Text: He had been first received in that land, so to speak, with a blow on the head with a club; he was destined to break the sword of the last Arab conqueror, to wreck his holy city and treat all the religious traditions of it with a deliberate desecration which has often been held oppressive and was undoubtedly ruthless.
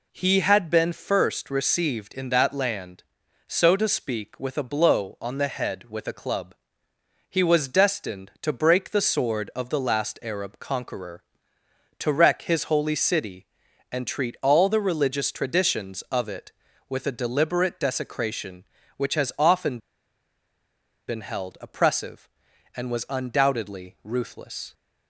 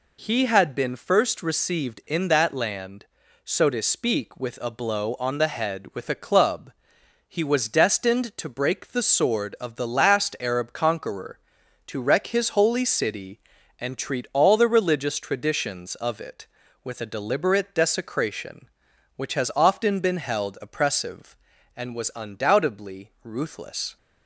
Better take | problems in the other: second | pauses between "often" and "been"; strong; at 19.7 s; 1.3 s long

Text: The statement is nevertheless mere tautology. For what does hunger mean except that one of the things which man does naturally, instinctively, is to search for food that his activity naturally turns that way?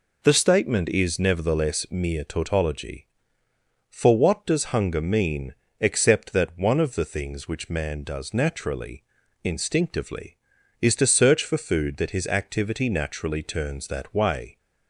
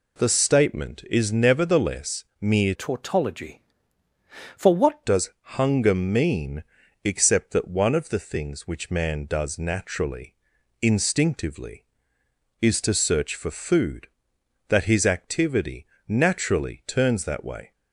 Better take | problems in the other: first | pauses between "nevertheless" and "mere"; slight; at 2.2 s; 0.16 s long // changes voice from "tautology" to "what"; from 2.7 to 5.0 s; 2.3 s long // pauses between "does" and "hunger"; slight; at 5.3 s; 0.26 s long // pauses between "mean" and "except"; at 6.6 s; 0.40 s long; slight in the first // pauses between "activity" and "naturally"; slight; at 15.8 s; 0.20 s long

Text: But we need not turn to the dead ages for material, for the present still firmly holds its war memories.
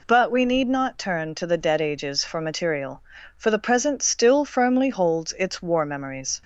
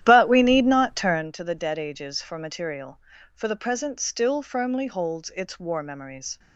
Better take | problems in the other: first | starts louder than the rest; strong; until 1.3 s; 11.5 dB

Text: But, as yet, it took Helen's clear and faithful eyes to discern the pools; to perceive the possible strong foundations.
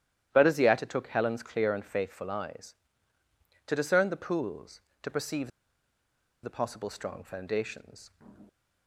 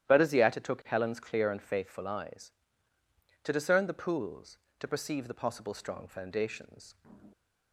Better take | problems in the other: second | starts louder than the rest; strong; until 1.3 s; 11.5 dB; strong in the second // pauses between "perceive" and "the"; noticeable; at 5.5 s; 0.93 s long

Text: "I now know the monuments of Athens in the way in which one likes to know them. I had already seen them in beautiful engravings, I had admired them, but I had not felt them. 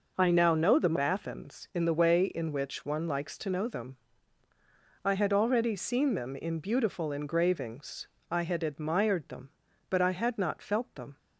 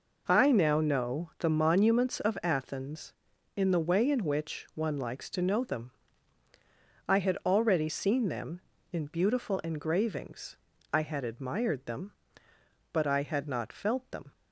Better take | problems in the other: second | skips "monuments of"; at 0.9 s

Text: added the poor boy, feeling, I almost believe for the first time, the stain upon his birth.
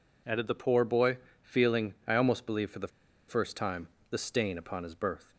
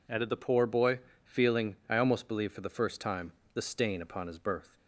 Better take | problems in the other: second | pauses between "the" and "first"; at 2.8 s; 0.40 s long

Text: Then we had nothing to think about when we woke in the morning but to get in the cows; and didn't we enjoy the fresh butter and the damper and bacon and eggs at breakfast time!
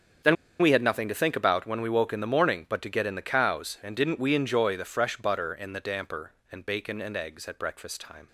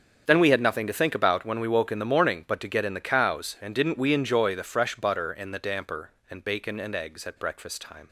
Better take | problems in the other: second | starts louder than the rest; strong; until 1.5 s; 8 dB; strong in the second // pauses between "Then" and "we"; slight; at 0.3 s; 0.25 s long

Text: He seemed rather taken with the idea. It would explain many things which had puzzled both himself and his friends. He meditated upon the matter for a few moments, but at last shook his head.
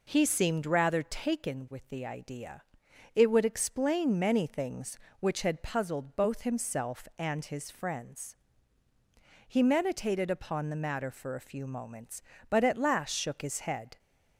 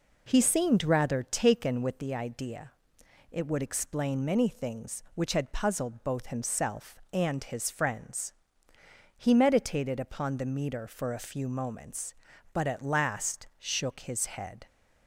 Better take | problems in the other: first | says "meter" for "matter"; at 10.4 s

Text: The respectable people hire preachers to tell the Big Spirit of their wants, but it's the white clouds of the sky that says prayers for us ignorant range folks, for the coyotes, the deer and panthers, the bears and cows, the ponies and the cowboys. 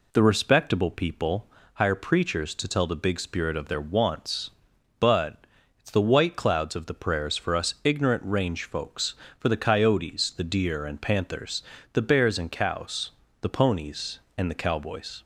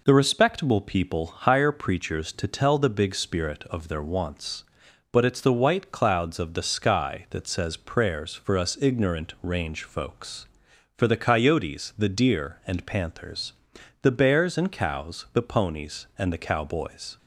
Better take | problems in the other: second | pauses between "people" and "hire"; slight; at 1.4 s; 0.28 s long // pauses between "but" and "it's"; at 5.3 s; 0.42 s long // skips "sky that says"; at 6.9 s

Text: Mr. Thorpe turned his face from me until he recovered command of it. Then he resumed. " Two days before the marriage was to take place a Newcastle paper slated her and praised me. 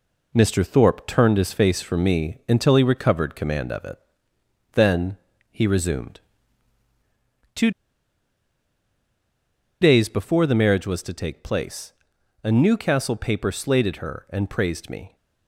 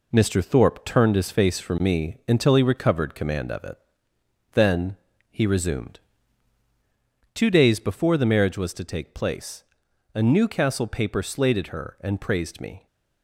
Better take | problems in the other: second | pauses between "Then" and "he"; slight; at 5.1 s; 0.34 s long; slight in the second // pauses between "Two" and "days"; strong; at 7.7 s; 2.1 s long // pauses between "place" and "a"; noticeable; at 11.9 s; 0.50 s long; noticeable in the second

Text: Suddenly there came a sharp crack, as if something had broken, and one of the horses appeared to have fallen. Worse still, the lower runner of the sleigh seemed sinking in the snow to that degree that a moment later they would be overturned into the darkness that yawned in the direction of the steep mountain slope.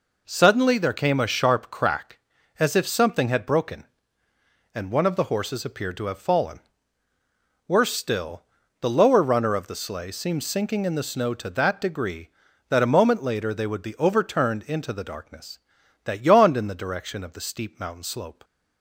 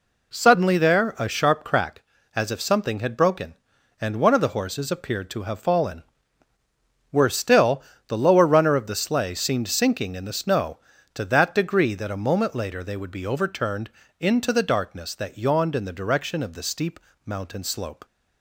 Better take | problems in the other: first | skips "came"; at 1.1 s // pauses between "overturned" and "into"; slight; at 13.9 s; 0.30 s long // pauses between "steep" and "mountain"; slight; at 17.0 s; 0.24 s long

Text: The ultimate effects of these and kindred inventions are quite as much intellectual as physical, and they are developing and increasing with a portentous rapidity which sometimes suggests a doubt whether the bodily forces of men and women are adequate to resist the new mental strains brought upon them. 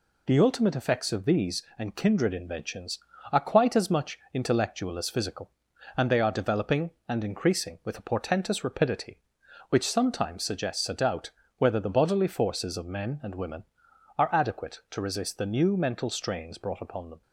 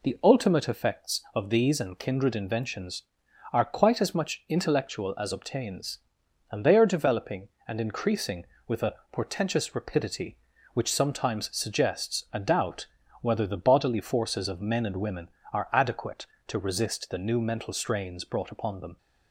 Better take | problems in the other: first | says "obtains" for "physical"; at 5.3 s // pauses between "a" and "portentous"; slight; at 8.9 s; 0.18 s long // pauses between "doubt" and "whether"; slight; at 12.8 s; 0.36 s long; slight in the first

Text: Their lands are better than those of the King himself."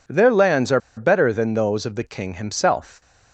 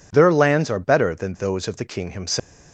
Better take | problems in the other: second | pauses between "are" and "better"; slight; at 0.7 s; 0.18 s long

